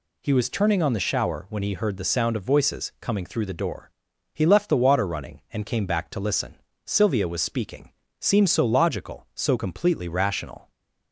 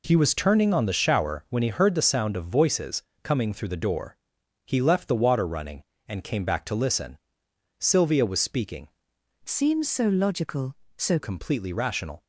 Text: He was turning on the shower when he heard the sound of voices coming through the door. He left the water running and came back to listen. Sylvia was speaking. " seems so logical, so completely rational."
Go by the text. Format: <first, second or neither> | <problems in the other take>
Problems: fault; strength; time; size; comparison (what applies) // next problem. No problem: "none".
first | pauses between "voices" and "coming"; slight; at 3.0 s; 0.22 s long // changes voice from "seems" to "so"; from 9.4 to 11.1 s; 1.7 s long